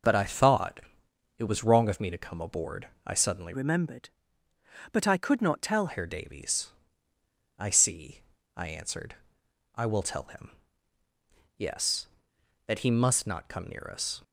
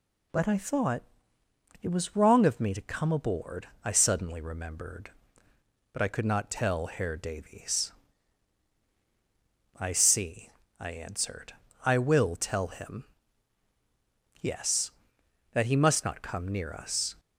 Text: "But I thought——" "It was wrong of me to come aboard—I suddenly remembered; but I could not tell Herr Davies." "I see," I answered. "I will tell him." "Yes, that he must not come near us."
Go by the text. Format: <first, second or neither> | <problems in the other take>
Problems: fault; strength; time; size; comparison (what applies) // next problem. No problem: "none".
second | changes voice from "remembered" to "tell"; from 3.5 to 5.8 s; 2.3 s long